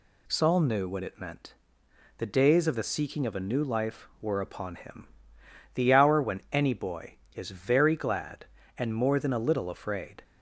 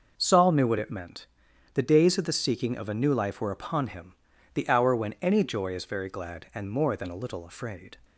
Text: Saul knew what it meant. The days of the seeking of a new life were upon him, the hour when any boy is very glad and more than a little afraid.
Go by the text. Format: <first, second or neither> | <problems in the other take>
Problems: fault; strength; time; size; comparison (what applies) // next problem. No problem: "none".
first | says "joy" for "boy"; at 5.4 s